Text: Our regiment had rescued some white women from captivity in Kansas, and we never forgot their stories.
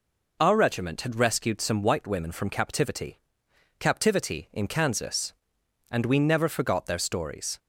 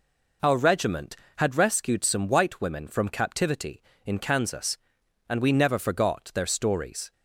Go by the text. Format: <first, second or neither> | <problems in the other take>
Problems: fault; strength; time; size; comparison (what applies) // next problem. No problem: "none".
second | says "captivity" twice; at 3.7 s